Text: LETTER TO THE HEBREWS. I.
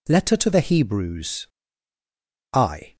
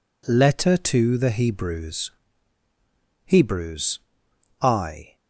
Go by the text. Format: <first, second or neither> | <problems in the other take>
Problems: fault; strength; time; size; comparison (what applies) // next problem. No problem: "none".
first | says "HEBREWS" twice; at 3.2 s